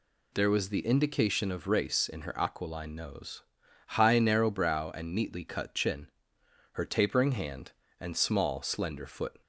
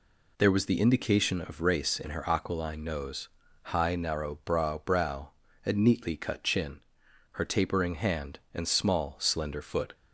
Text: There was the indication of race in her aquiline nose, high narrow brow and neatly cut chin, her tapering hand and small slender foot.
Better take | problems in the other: first | says "brow" twice; at 4.8 s

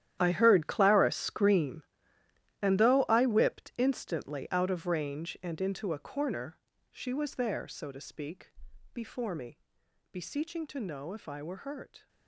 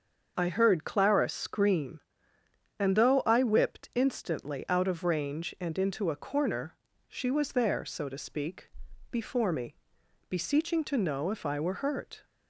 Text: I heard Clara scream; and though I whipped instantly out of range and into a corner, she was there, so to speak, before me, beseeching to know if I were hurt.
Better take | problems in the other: second | gets quieter; strong; throughout; 15 dB // starts louder than the rest; strong; until 1.2 s; 11 dB; also in the second

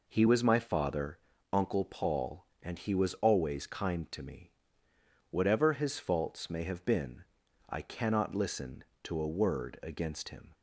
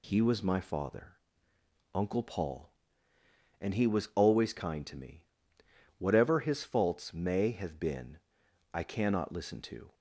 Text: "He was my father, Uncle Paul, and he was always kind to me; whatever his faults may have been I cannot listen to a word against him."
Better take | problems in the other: first | pauses between "been" and "I"; noticeable; at 8.1 s; 0.56 s long; noticeable in the first // stops before "a word against him"; at 9.9 s

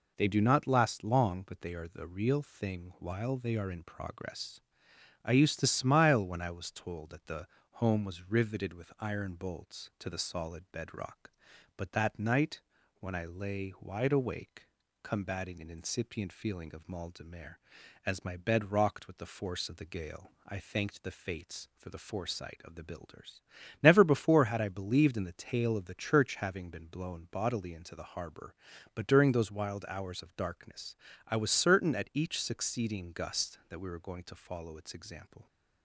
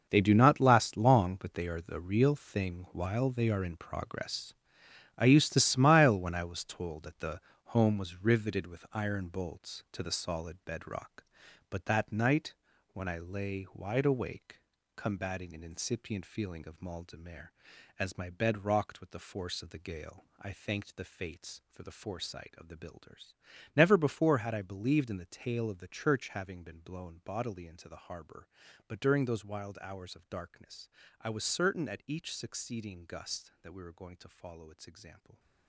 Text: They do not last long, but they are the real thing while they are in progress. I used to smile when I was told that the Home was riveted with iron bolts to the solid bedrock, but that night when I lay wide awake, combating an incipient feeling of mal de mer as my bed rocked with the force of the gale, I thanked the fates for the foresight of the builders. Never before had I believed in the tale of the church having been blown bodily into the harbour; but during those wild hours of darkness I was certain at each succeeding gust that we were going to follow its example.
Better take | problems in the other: first | gets quieter; strong; throughout; 12.5 dB // pauses between "the" and "Home"; slight; at 7.3 s; 0.32 s long; slight in the first // pauses between "night" and "when"; at 12.5 s; 0.40 s long; also in the first // pauses between "darkness" and "I"; slight; at 30.8 s; 0.32 s long; slight in the first

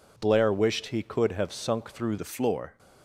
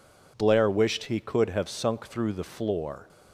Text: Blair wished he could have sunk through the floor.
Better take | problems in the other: second | changes voice at "the"; from 2.1 s on; 0.6 s long

